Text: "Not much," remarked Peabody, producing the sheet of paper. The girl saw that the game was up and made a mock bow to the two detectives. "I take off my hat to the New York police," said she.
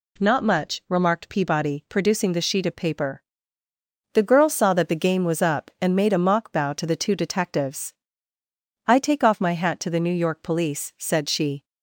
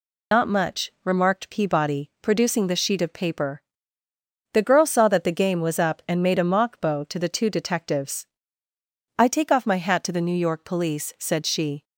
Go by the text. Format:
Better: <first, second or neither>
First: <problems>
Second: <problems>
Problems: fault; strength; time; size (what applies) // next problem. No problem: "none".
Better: first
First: none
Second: loses the start of "Not"; at 0.3 s; 115 ms